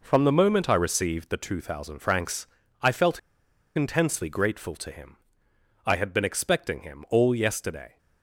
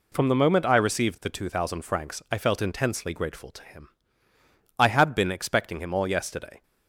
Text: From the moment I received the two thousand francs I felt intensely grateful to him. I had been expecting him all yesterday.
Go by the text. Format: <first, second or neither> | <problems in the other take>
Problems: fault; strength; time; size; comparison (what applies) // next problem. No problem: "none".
second | pauses between "francs" and "I"; slight; at 2.4 s; 0.36 s long // pauses between "felt" and "intensely"; noticeable; at 3.1 s; 0.57 s long